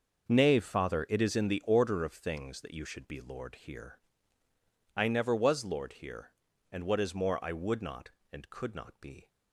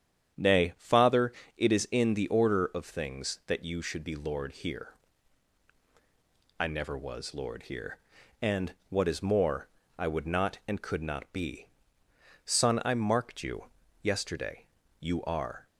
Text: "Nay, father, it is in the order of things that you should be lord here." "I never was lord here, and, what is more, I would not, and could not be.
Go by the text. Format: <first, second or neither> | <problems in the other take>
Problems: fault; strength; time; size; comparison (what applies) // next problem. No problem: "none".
first | starts louder than the rest; strong; until 1.6 s; 9 dB; noticeable in the first // goes on to say "Son I marked you yesterday You are"; strong; from 12.4 s on; 3.2 s long